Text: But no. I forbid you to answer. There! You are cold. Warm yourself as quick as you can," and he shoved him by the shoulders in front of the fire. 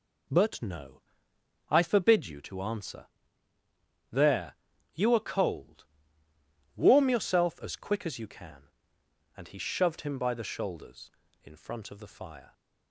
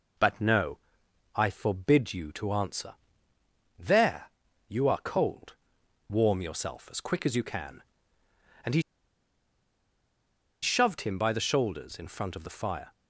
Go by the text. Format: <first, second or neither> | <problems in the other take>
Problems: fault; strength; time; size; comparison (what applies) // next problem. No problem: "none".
first | pauses between "he" and "shoved"; strong; at 8.8 s; 1.8 s long